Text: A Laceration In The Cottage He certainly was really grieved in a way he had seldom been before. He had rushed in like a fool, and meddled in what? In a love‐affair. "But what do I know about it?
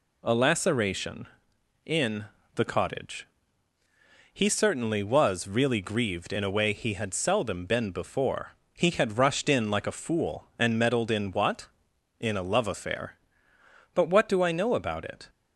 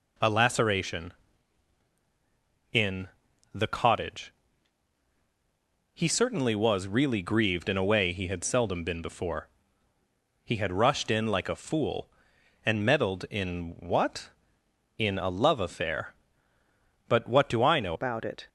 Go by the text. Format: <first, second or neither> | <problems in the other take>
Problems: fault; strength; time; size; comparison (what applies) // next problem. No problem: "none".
first | pauses between "In" and "The"; at 3.0 s; 0.44 s long; slight in the first // pauses between "Cottage" and "He"; strong; at 4.3 s; 1.6 s long; also in the first // changes voice at "about"; from 17.9 s on; 0.5 s long